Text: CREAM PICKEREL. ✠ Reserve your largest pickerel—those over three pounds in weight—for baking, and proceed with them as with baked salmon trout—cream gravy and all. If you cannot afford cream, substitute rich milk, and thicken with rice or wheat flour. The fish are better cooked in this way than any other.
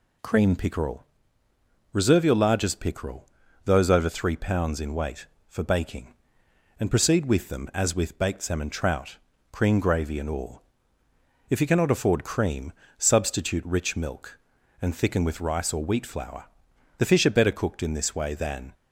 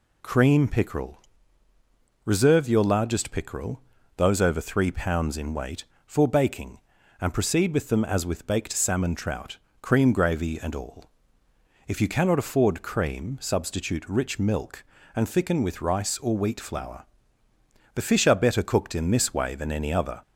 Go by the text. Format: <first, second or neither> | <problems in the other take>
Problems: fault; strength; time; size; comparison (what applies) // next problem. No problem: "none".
second | stops before "any other"; at 18.7 s